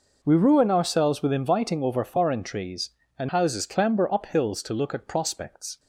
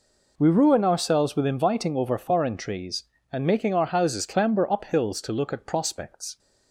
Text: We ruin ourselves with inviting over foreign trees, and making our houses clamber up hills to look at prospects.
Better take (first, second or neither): second